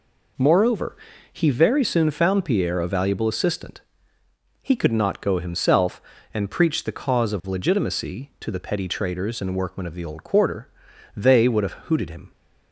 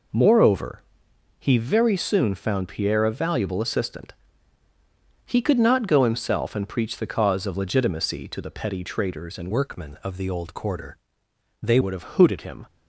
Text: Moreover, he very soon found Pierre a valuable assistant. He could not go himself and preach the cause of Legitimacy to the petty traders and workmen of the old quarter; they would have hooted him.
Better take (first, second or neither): first